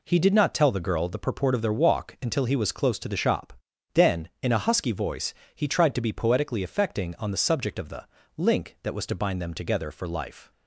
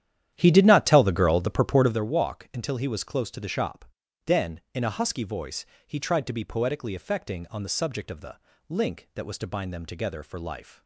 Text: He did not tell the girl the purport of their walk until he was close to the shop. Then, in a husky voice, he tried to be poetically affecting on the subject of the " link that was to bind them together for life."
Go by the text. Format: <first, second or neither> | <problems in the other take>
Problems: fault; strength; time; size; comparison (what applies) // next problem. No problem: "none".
first | starts louder than the rest; strong; until 2.1 s; 11 dB